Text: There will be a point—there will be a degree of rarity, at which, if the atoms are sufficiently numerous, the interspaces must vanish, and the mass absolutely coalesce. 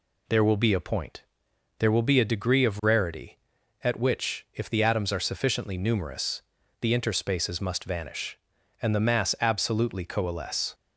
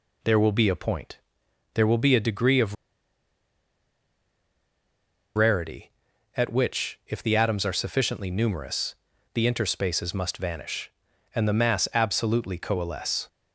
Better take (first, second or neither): first